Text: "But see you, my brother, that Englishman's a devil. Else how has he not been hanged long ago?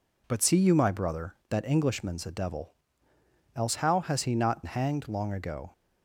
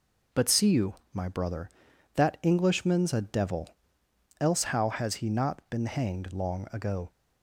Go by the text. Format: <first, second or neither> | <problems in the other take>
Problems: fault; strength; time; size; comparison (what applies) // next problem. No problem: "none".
second | skips "been"; at 4.6 s